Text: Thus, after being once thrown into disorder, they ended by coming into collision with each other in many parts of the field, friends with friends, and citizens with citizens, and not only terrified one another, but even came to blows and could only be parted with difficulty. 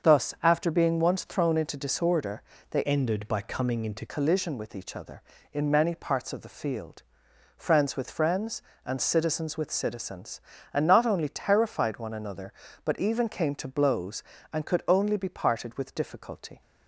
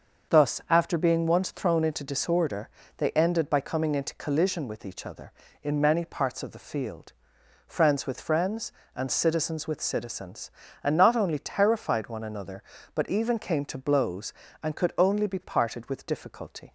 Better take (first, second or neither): second